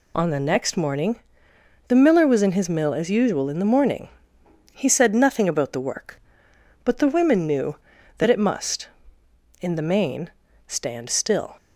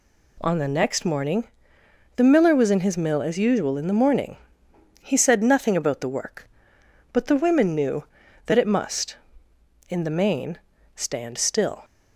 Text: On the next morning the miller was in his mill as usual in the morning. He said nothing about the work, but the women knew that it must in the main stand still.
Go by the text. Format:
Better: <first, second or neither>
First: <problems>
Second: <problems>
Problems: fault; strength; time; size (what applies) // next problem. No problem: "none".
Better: second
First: loses the start of "On"; at 0.1 s; 55 ms // pauses between "morning" and "the"; noticeable; at 1.2 s; 0.66 s long // pauses between "main" and "stand"; slight; at 10.3 s; 0.36 s long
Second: pauses between "morning" and "the"; noticeable; at 1.4 s; 0.66 s long // pauses between "main" and "stand"; slight; at 10.5 s; 0.36 s long